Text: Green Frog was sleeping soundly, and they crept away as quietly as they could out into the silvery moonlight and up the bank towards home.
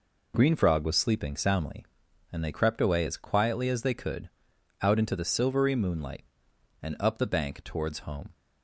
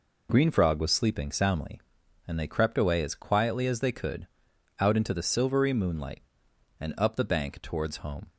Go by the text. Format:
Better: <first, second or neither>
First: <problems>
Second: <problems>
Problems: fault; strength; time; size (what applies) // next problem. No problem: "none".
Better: neither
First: pauses between "could" and "out"; noticeable; at 4.3 s; 0.50 s long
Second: pauses between "could" and "out"; noticeable; at 4.2 s; 0.50 s long